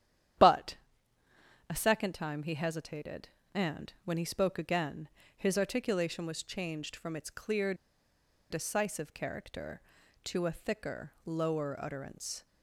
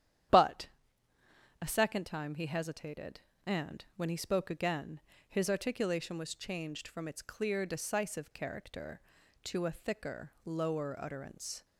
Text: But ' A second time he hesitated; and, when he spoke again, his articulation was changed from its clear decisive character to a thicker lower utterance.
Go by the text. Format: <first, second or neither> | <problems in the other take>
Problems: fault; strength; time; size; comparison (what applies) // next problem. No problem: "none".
second | starts louder than the rest; strong; until 1.8 s; 9 dB; strong in the second // pauses between "clear" and "decisive"; noticeable; at 7.7 s; 0.76 s long